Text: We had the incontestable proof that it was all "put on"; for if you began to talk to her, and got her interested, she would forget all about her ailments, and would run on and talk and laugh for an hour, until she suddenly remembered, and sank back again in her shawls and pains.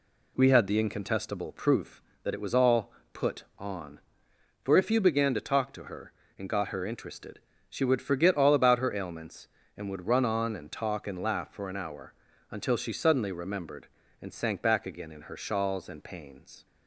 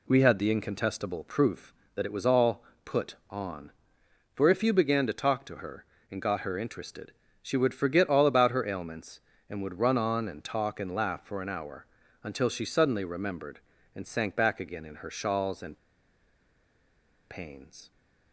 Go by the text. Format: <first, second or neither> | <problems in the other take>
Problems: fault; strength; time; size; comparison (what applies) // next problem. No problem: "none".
first | pauses between "all" and "put"; slight; at 2.6 s; 0.22 s long; slight in the first // pauses between "and" and "pains"; strong; at 15.7 s; 1.5 s long